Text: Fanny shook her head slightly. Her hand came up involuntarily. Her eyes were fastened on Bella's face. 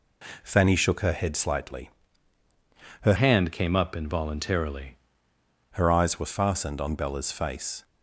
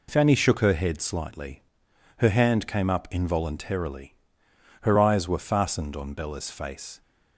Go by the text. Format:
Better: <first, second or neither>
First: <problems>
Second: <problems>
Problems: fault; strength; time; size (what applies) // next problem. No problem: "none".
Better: second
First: changes voice from "hand" to "involuntarily"; from 3.1 to 4.9 s; 1.8 s long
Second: none